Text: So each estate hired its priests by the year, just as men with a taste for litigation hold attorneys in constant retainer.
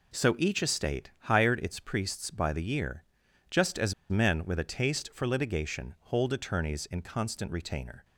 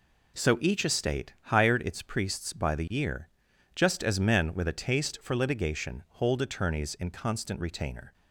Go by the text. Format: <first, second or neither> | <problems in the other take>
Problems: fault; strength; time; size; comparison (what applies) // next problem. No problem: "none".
second | pauses between "as" and "men"; slight; at 3.9 s; 0.16 s long